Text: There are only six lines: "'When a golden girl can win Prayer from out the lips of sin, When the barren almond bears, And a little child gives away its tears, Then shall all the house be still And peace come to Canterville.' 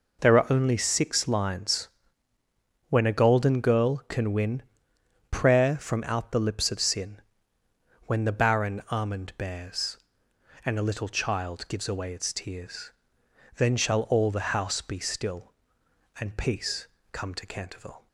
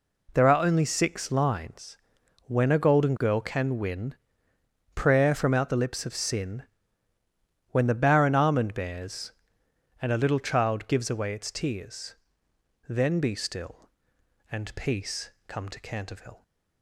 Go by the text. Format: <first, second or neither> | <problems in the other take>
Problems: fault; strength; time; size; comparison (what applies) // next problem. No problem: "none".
first | pauses between "win" and "Prayer"; noticeable; at 4.1 s; 0.80 s long; noticeable in the first // skips "shall all the house"; at 13.2 s // pauses between "peace" and "come"; slight; at 15.3 s; 0.18 s long; slight in the first